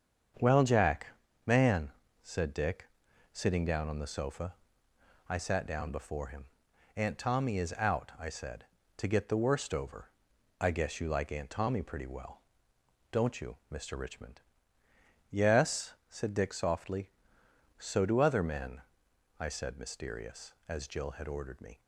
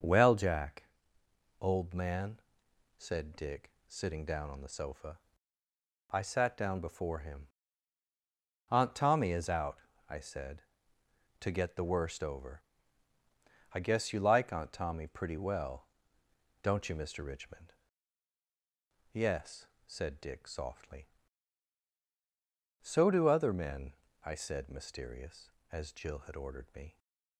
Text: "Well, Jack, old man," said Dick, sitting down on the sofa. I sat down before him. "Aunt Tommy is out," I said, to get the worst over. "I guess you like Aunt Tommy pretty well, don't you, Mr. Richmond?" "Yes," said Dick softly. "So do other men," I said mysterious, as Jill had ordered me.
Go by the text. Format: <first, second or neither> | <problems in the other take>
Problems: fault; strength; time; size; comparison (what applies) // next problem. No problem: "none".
second | starts louder than the rest; strong; until 1.7 s; 7.5 dB; also in the second // skips "old"; at 1.2 s